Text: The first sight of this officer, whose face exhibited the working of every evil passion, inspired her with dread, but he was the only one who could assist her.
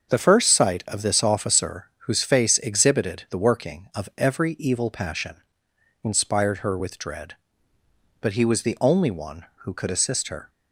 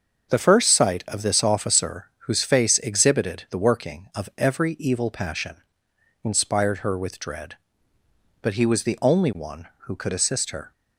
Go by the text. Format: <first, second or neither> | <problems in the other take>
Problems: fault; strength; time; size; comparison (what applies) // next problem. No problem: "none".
neither | starts louder than the rest; the same in both